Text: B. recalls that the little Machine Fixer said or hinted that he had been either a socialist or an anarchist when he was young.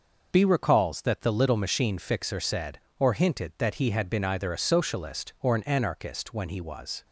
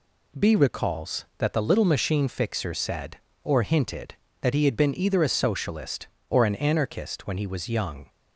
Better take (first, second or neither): second